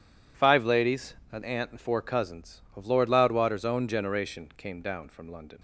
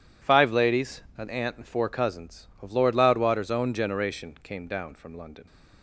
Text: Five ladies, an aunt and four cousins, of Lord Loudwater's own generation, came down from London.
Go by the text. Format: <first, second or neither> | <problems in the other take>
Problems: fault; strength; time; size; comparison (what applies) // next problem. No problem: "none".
neither | none